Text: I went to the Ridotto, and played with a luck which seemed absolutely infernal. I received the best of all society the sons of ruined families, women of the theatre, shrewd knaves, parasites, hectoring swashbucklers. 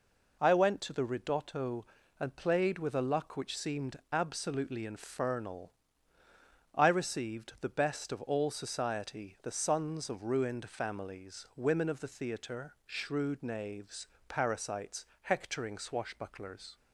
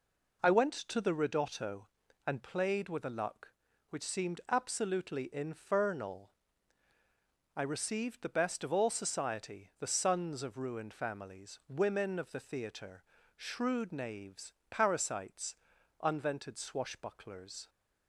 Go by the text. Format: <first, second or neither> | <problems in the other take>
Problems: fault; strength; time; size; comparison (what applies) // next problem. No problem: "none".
first | says "unvented" for "hectoring"; at 16.0 s